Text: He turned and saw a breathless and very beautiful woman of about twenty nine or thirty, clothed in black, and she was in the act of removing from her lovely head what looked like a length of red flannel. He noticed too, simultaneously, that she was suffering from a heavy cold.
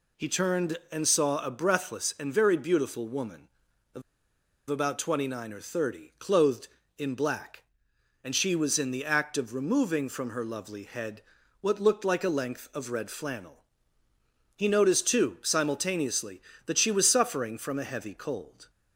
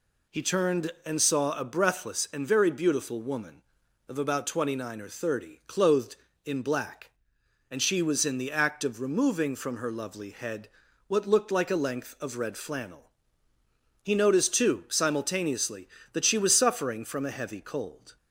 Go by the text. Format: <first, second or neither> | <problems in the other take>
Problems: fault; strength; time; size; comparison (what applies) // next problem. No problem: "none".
second | pauses between "of" and "about"; noticeable; at 4.0 s; 0.68 s long // pauses between "head" and "what"; at 11.2 s; 0.38 s long; also in the second